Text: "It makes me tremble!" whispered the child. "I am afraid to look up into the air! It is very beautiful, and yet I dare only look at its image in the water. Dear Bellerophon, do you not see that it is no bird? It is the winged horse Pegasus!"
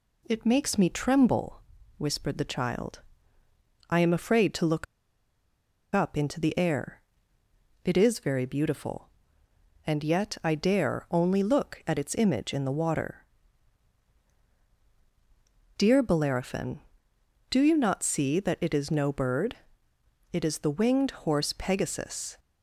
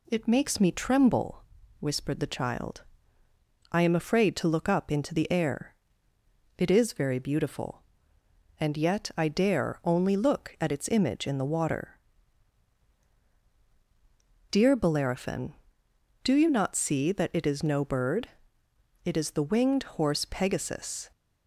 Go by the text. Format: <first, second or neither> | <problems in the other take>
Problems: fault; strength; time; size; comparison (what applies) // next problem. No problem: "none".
second | pauses between "look" and "up"; at 4.8 s; 1.0 s long